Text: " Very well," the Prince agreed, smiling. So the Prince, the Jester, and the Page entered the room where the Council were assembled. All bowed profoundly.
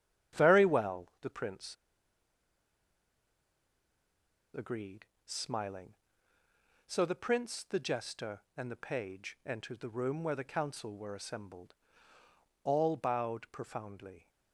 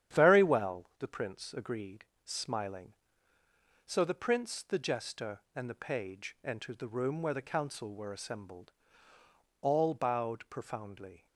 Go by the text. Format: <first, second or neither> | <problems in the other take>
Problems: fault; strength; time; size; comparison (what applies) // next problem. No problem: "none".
second | starts louder than the rest; strong; until 1.4 s; 10 dB; strong in the second // pauses between "Prince" and "agreed"; strong; at 1.7 s; 2.7 s long